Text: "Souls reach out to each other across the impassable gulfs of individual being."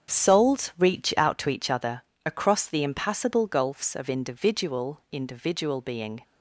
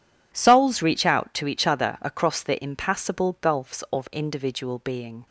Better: second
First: starts louder than the rest; strong; until 1.2 s; 8 dB // pauses between "other" and "across"; slight; at 2.0 s; 0.24 s long // says "individual" twice; at 5.1 s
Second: none

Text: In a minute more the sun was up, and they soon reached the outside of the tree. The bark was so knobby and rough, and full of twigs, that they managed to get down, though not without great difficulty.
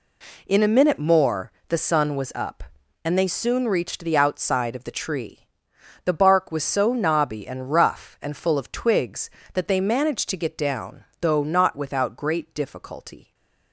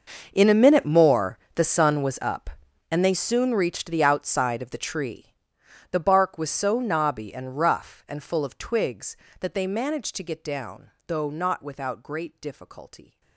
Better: first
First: pauses between "more" and "the"; slight; at 1.5 s; 0.16 s long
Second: gets quieter; strong; throughout; 19.5 dB // pauses between "more" and "the"; slight; at 1.3 s; 0.16 s long

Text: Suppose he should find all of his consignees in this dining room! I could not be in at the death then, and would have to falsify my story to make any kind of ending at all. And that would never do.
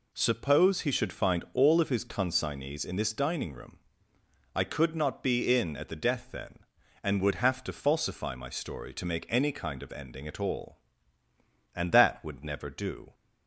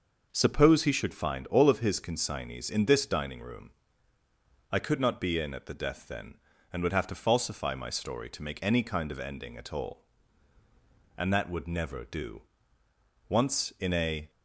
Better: first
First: none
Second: goes on to say "Once in a"; noticeable; from 13.2 s on; 1.0 s long

